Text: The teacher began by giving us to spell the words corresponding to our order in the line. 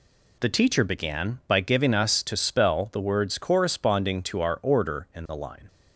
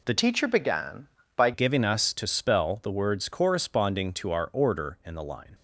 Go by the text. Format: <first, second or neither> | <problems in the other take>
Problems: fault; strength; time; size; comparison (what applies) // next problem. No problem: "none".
first | changes voice from "teacher" to "by"; from 0.1 to 1.5 s; 1.4 s long